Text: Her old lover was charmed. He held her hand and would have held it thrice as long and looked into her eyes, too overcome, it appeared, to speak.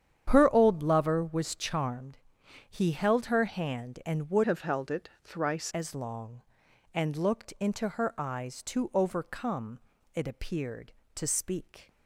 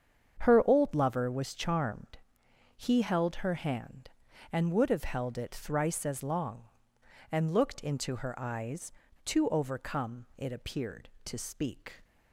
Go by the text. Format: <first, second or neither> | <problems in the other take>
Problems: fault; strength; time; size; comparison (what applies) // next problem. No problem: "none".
second | starts louder than the rest; strong; until 1.2 s; 9 dB; strong in the second // changes voice from "have" to "thrice"; from 4.4 to 5.7 s; 1.3 s long